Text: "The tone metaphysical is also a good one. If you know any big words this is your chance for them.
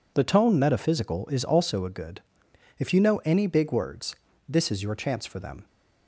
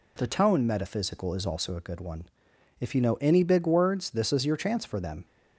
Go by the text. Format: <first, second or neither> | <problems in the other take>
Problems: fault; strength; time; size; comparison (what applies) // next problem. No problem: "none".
second | skips "one"; at 2.4 s // pauses between "words" and "this"; slight; at 4.1 s; 0.34 s long